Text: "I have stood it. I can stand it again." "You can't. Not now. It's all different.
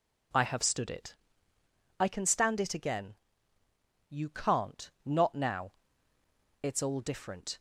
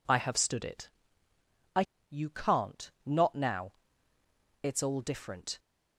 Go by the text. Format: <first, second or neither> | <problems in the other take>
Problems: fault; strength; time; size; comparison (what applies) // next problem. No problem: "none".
first | skips "can stand it again"; at 1.9 s